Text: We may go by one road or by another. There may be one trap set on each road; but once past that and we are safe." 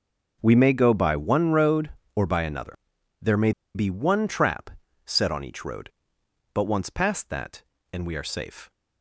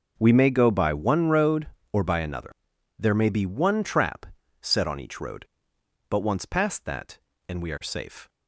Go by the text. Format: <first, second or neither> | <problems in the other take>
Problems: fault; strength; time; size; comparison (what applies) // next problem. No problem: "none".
second | pauses between "may" and "be"; slight; at 3.5 s; 0.24 s long // pauses between "trap" and "set"; slight; at 4.6 s; 0.36 s long; slight in the second